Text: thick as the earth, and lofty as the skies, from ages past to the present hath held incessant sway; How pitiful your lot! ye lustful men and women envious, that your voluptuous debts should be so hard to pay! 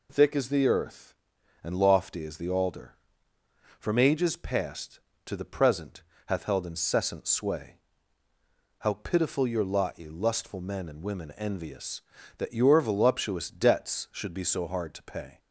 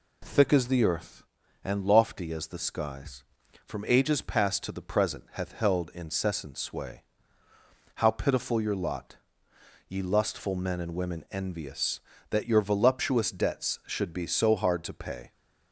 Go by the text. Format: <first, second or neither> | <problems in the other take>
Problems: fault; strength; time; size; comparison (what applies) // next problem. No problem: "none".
second | says "alder" for "skies"; at 2.4 s // pauses between "present" and "hath"; slight; at 6.0 s; 0.24 s long